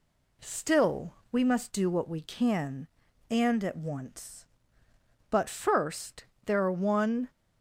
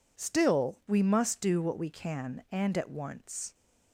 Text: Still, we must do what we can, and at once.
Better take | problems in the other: second | goes on to say "But first there are one"; strong; from 5.2 s on; 2.0 s long

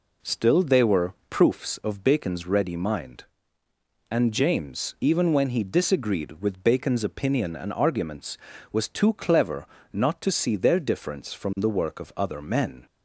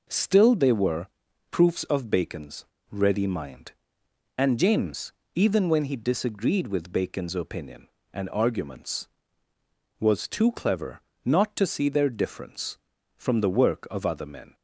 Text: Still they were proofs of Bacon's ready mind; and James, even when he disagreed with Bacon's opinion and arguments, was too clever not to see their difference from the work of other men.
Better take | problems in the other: first | pauses between "were" and "proofs"; at 1.0 s; 0.44 s long; slight in the first // pauses between "Bacon's" and "ready"; slight; at 2.6 s; 0.26 s long // pauses between "clever" and "not"; slight; at 11.0 s; 0.26 s long; slight in the first

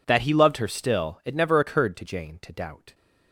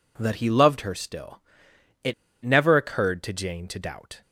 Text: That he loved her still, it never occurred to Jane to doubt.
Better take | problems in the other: first | pauses between "it" and "never"; slight; at 2.1 s; 0.31 s long

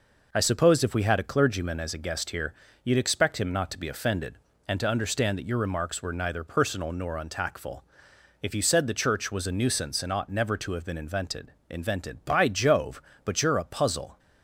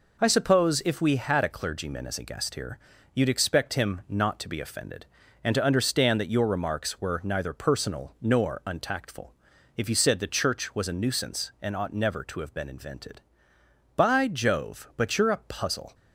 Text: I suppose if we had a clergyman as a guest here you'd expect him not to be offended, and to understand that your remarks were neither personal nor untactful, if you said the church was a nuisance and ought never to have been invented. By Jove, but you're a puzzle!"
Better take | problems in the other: second | pauses between "here" and "you'd"; slight; at 2.5 s; 0.32 s long; slight in the second // says "invented" twice; at 11.6 s

